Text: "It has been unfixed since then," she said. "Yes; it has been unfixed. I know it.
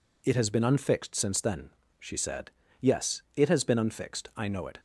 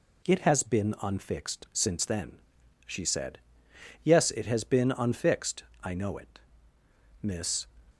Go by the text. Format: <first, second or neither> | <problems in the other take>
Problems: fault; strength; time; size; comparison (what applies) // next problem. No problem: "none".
first | goes on to say "Miss"; slight; from 7.2 s on; 0.46 s long